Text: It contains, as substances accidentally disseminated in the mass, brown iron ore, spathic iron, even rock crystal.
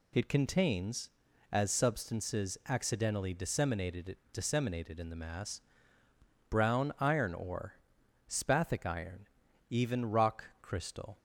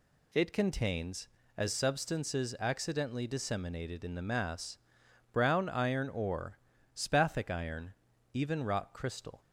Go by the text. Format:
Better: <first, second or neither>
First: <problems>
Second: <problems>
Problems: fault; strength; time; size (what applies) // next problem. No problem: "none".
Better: second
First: says "disseminated" twice; at 4.3 s // pauses between "rock" and "crystal"; slight; at 10.4 s; 0.18 s long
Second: none